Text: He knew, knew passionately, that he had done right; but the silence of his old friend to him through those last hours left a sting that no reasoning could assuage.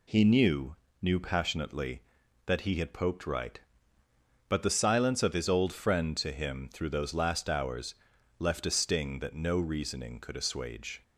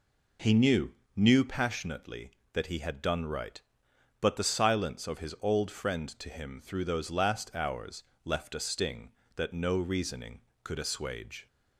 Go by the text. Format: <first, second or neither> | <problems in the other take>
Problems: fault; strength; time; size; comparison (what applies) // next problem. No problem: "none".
second | says "poked" for "done"; at 2.9 s // pauses between "hours" and "left"; noticeable; at 7.9 s; 0.46 s long; slight in the second